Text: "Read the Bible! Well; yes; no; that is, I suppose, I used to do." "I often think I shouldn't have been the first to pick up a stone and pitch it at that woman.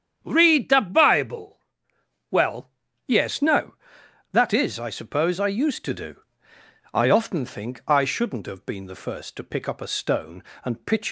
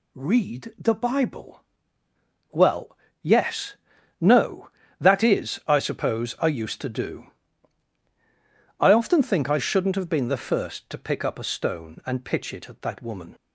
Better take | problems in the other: second | starts louder than the rest; strong; until 1.2 s; 8.5 dB // stops before "it at that woman"; at 11.0 s

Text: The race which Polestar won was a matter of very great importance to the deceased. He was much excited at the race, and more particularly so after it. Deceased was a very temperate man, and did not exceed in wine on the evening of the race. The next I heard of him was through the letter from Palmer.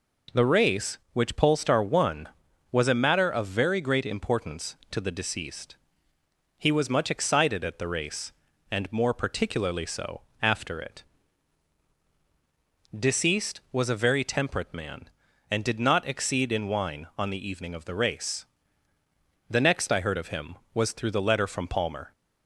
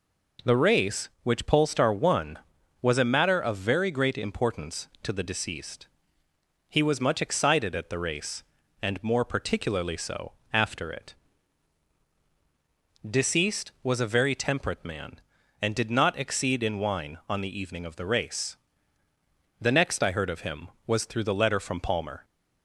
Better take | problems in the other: neither | pauses between "so" and "after"; slight; the same in both

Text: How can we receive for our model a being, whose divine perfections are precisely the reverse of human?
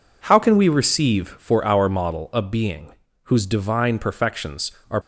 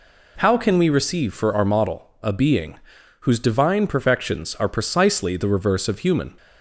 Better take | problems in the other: second | stops before "precisely the reverse of human"; at 5.0 s

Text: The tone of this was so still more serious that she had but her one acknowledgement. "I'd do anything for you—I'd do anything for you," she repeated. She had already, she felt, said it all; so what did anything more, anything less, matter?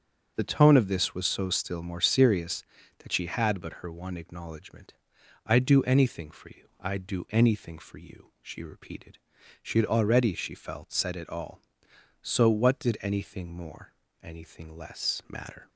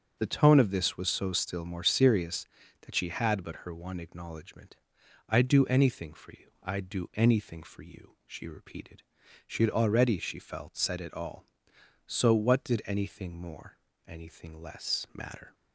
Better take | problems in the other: neither | starts louder than the rest; strong; the same in both

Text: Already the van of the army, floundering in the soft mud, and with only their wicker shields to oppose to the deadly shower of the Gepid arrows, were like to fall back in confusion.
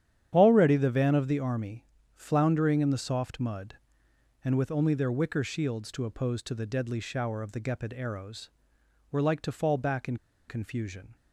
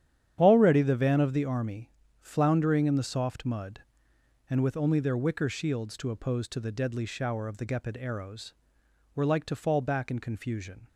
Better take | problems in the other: second | starts louder than the rest; strong; until 1.3 s; 9.5 dB; strong in the second // pauses between "in" and "confusion"; slight; at 10.1 s; 0.32 s long

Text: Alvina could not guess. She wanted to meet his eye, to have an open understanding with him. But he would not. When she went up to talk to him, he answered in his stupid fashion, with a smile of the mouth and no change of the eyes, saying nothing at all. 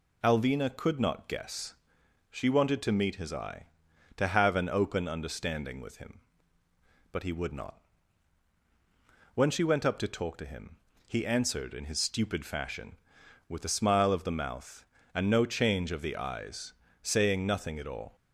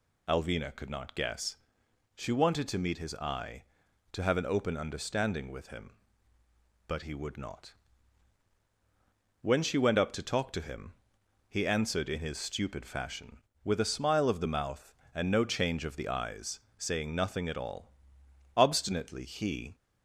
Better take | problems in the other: first | goes on to say "Obstinately he"; noticeable; from 18.5 s on; 1.1 s long

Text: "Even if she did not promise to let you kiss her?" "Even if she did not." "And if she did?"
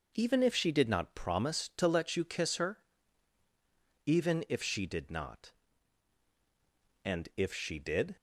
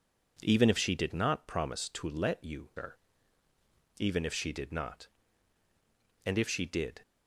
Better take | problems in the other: first | skips "kiss"; at 2.7 s

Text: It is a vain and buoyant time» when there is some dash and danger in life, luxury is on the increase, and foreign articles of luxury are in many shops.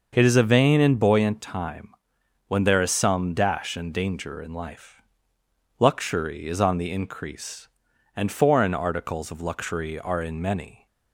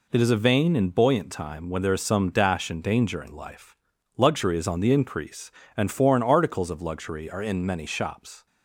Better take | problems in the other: second | pauses between "time" and "when"; noticeable; at 1.8 s; 0.56 s long // stops before "shops"; at 10.8 s

